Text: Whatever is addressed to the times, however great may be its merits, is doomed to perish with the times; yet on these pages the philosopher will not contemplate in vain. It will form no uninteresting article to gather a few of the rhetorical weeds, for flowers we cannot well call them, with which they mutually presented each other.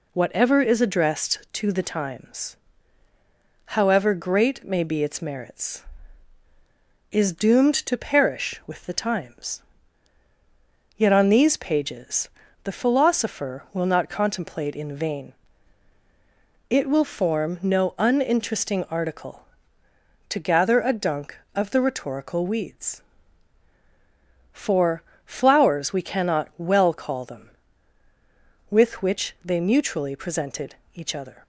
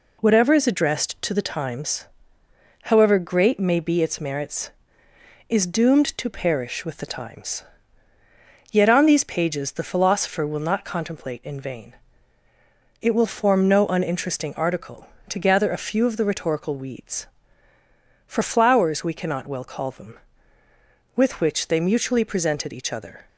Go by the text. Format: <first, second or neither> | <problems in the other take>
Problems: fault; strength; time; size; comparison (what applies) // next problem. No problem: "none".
second | pauses between "pages" and "the"; slight; at 12.2 s; 0.36 s long // says "dunk" for "few"; at 20.9 s // pauses between "for" and "flowers"; slight; at 25.0 s; 0.24 s long // pauses between "presented" and "each"; slight; at 30.7 s; 0.20 s long